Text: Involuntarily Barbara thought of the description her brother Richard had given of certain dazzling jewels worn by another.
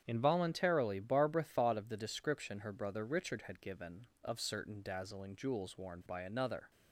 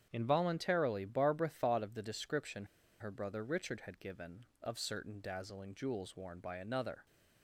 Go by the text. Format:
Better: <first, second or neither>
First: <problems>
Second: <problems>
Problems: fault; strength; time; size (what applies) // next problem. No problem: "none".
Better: first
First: starts louder than the rest; strong; until 1.0 s; 8.5 dB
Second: starts louder than the rest; strong; until 1.1 s; 8.5 dB // pauses between "description" and "her"; slight; at 2.6 s; 0.35 s long